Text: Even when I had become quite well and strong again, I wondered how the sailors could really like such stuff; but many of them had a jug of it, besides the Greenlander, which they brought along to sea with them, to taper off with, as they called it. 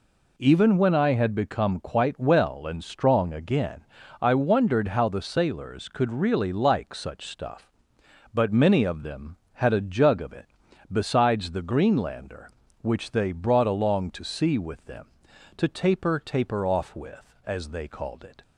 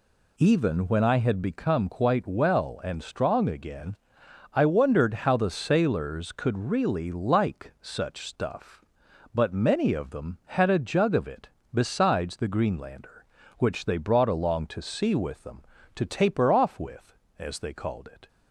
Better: second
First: says "taper" twice; at 16.1 s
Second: none

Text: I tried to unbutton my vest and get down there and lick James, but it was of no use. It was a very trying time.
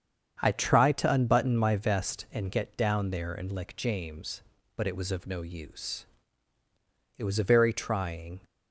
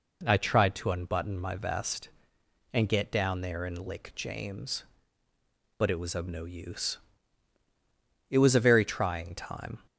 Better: second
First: starts louder than the rest; strong; until 1.4 s; 7.5 dB // stops before "time"; at 8.4 s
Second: none

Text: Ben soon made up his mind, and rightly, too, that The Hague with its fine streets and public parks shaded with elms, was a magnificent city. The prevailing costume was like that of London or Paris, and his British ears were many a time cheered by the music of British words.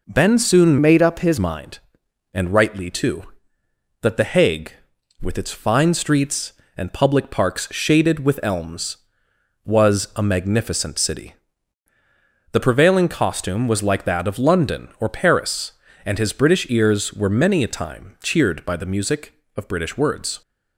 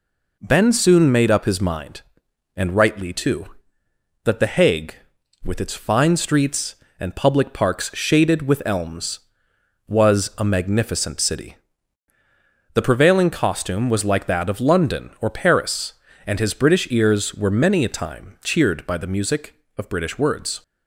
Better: second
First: changes voice from "made" to "his"; from 0.8 to 1.3 s; 0.5 s long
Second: none

